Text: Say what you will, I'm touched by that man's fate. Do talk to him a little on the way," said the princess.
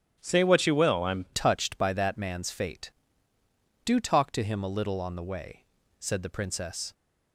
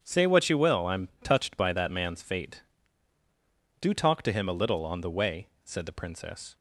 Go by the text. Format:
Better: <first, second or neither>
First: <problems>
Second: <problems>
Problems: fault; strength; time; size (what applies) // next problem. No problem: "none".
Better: second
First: starts louder than the rest; strong; until 1.2 s; 9 dB // changes voice at "touched"; from 1.3 s on; 5.6 s long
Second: starts louder than the rest; strong; until 1.0 s; 8 dB